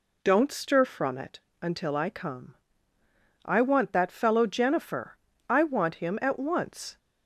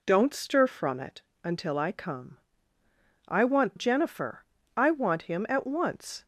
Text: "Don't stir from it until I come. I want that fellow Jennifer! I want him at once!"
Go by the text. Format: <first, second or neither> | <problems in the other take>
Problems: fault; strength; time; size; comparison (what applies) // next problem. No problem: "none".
first | pauses between "it" and "until"; slight; at 1.2 s; 0.22 s long; slight in the first // skips "that fellow"; at 3.7 s